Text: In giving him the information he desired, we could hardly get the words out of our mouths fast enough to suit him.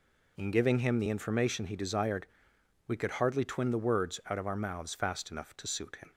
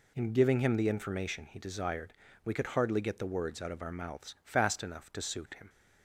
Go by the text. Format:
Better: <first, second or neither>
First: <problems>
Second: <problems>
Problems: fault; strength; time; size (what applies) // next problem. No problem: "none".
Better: second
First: says "twin" for "get"; at 3.4 s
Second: none